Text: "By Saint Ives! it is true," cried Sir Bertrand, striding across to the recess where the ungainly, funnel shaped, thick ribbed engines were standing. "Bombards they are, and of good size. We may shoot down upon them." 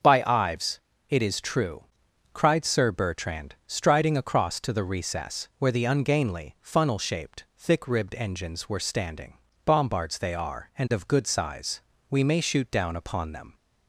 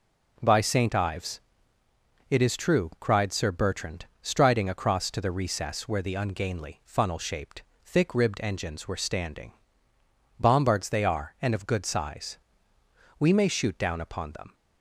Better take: second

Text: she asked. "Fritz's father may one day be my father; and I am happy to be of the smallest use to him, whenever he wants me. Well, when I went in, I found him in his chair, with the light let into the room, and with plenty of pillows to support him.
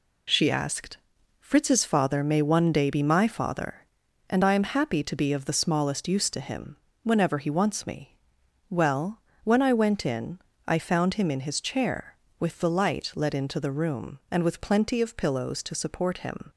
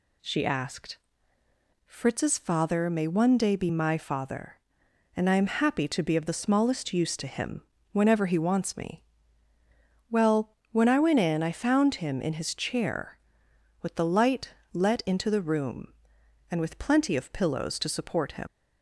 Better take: first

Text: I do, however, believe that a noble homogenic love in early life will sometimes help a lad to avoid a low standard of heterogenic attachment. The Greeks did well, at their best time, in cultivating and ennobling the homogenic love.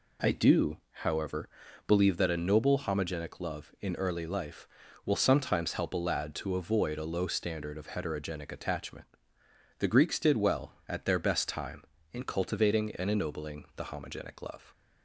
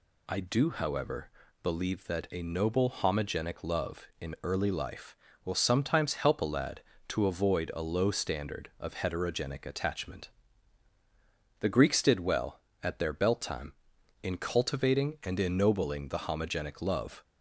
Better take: first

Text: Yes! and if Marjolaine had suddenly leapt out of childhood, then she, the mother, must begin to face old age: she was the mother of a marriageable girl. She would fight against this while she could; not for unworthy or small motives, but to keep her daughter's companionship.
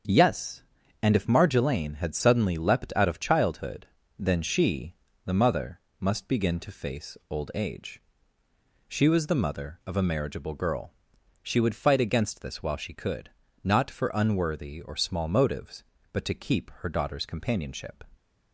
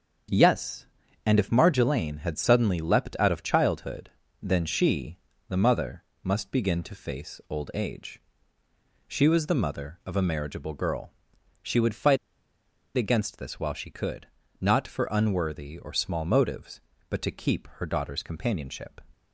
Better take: first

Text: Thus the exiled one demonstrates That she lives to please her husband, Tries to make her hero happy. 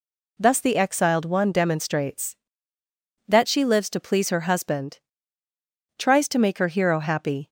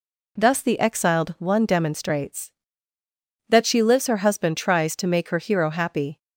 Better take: first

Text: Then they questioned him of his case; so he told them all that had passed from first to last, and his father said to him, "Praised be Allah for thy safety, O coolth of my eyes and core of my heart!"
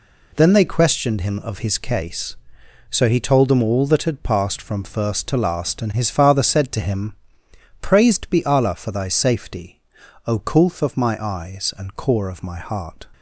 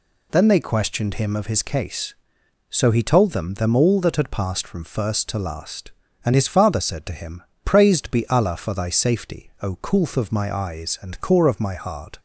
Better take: first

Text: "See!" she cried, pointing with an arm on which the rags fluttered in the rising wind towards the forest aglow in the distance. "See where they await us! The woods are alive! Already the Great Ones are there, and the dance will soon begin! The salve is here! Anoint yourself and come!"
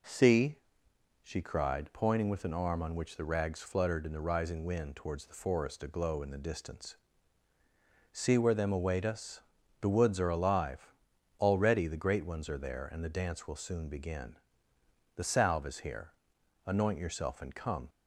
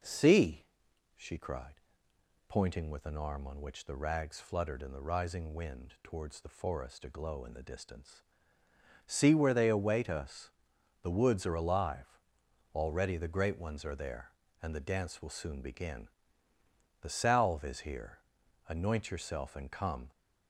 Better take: second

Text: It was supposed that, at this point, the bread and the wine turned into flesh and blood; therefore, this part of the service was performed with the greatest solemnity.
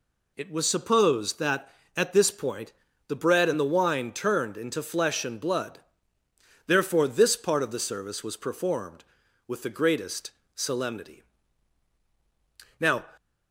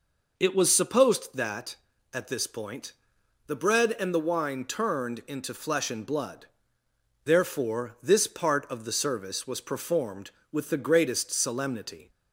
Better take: second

